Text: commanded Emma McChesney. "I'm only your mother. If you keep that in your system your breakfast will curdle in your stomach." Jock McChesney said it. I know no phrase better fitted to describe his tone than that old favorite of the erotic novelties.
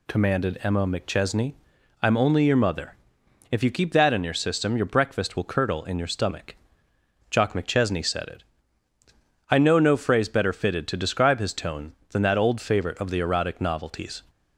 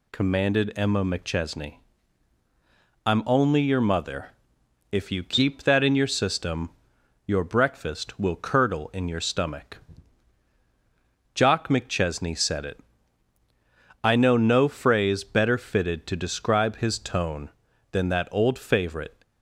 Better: first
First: none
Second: pauses between "system" and "your"; noticeable; at 6.7 s; 0.56 s long // stops before "of the erotic novelties"; at 19.2 s

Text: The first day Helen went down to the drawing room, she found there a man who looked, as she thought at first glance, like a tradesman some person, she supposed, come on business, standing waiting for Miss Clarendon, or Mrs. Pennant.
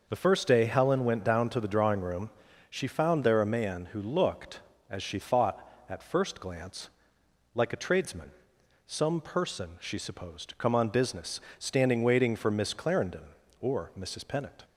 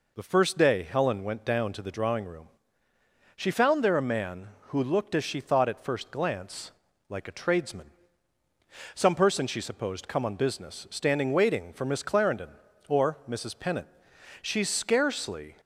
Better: first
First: pauses between "tradesman" and "some"; noticeable; at 8.3 s; 0.58 s long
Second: pauses between "tradesman" and "some"; at 7.8 s; 1.0 s long // goes on to say "She scarcely"; noticeable; from 14.4 s on; 1.1 s long

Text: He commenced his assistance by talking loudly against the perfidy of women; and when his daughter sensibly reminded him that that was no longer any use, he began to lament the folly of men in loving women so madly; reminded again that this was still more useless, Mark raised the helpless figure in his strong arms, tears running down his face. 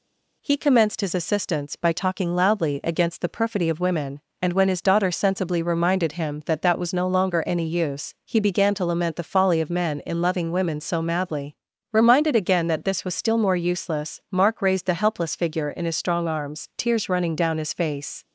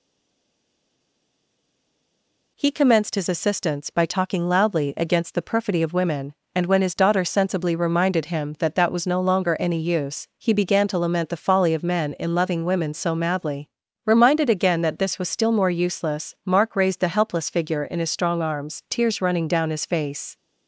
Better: first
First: none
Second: stays silent before the first word; strong; until 2.5 s; 2.5 s long

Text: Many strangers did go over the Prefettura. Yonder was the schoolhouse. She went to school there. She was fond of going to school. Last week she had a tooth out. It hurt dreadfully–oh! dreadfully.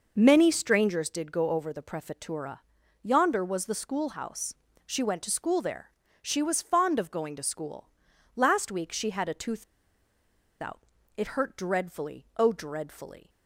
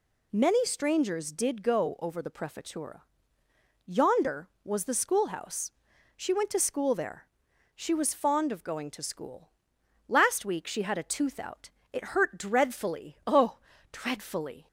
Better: second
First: pauses between "tooth" and "out"; at 9.6 s; 0.98 s long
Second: none

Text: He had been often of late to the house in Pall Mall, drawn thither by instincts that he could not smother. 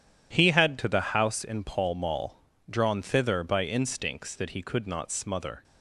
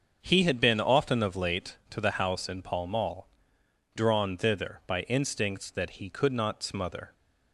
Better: second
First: starts louder than the rest; strong; until 1.3 s; 10.5 dB // skips "been often of late"; at 0.7 s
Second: starts louder than the rest; until 1.2 s; 6.5 dB

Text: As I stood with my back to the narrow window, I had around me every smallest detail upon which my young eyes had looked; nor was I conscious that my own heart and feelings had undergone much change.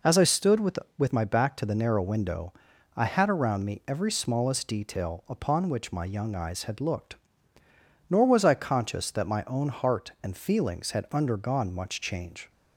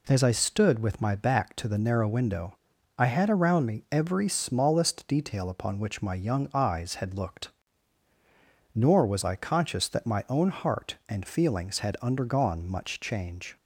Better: second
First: says "with" twice; at 0.9 s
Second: none

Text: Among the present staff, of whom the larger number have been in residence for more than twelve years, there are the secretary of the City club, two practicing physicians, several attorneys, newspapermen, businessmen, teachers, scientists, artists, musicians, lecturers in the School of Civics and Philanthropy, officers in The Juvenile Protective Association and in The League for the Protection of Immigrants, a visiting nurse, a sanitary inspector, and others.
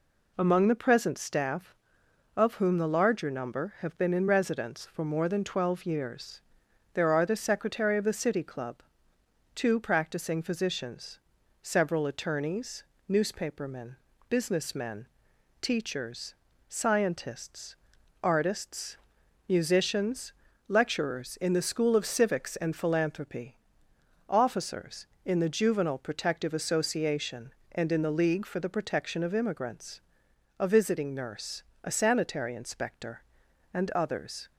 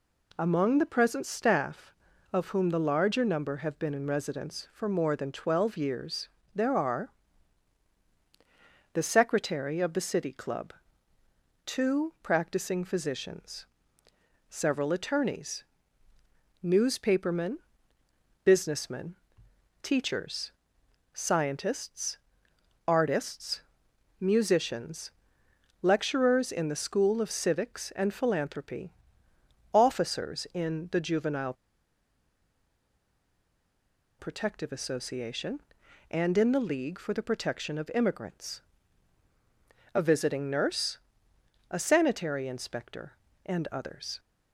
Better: first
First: none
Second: pauses between "are" and "the"; strong; at 7.0 s; 1.8 s long // pauses between "Juvenile" and "Protective"; strong; at 31.5 s; 2.6 s long

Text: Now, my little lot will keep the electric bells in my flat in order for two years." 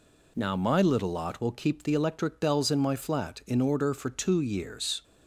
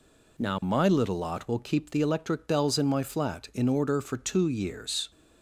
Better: neither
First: none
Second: none

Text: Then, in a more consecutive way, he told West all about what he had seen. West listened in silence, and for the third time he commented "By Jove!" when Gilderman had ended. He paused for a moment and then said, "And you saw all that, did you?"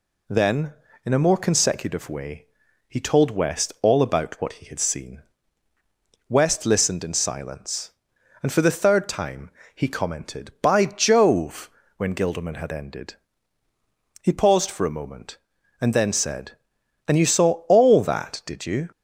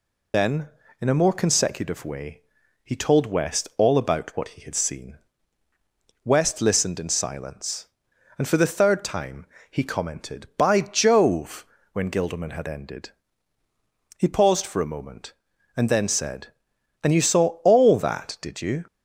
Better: first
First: pauses between "time" and "he"; slight; at 9.5 s; 0.24 s long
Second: loses the start of "Then"; at 0.3 s; 100 ms // pauses between "time" and "he"; slight; at 9.4 s; 0.24 s long

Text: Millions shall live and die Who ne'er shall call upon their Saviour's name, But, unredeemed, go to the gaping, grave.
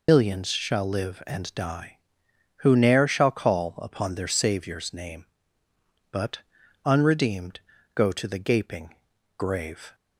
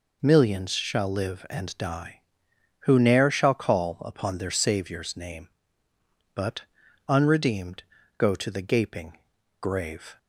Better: second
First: loses the start of "Millions"; at 0.0 s; 100 ms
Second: none

